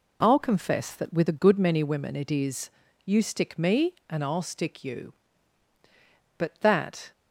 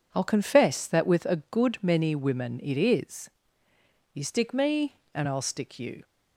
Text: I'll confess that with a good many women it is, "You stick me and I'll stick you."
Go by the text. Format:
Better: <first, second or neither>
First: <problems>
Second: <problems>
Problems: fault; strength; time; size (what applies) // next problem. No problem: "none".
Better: second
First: goes on to say "But that"; noticeable; from 6.3 s on; 0.74 s long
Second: none